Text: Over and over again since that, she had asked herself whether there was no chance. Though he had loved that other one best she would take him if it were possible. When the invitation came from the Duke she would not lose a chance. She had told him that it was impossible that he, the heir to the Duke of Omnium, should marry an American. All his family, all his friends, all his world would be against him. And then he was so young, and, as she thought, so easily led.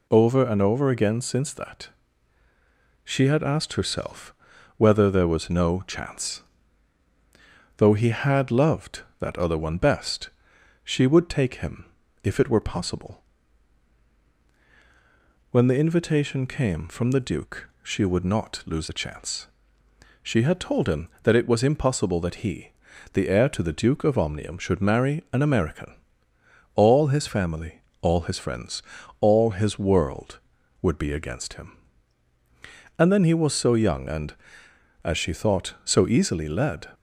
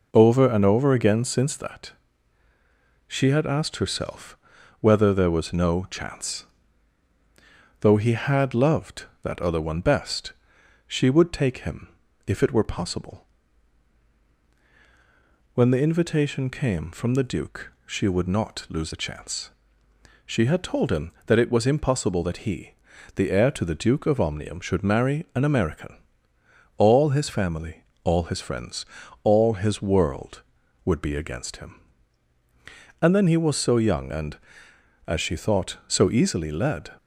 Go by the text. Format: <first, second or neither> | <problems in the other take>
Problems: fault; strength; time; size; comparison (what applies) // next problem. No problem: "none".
first | starts louder than the rest; noticeable; until 1.7 s; 5 dB // pauses between "herself" and "whether"; at 4.3 s; 0.44 s long; also in the first // pauses between "best" and "she"; noticeable; at 10.3 s; 0.54 s long; noticeable in the first // pauses between "him" and "if"; at 11.8 s; 0.38 s long; also in the first